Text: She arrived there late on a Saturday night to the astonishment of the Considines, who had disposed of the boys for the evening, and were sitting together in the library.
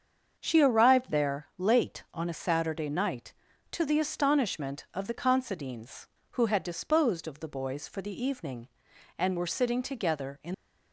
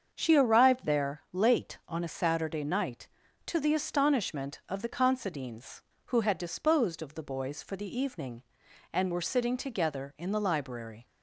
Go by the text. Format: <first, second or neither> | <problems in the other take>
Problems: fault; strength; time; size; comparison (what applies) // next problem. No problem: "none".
second | starts louder than the rest; until 1.4 s; 7 dB; also in the second // stops before "the library"; at 10.5 s